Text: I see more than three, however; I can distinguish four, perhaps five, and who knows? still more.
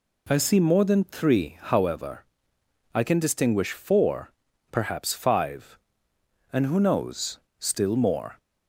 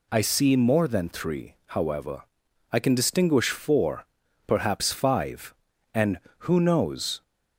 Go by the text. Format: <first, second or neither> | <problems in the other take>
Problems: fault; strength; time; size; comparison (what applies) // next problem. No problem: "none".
first | stops before "still more"; at 7.2 s